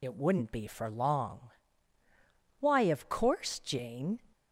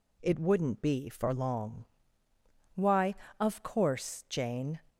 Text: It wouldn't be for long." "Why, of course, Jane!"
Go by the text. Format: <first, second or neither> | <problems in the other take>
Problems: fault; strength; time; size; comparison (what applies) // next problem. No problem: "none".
second | loses the start of "It"; at 0.0 s; 50 ms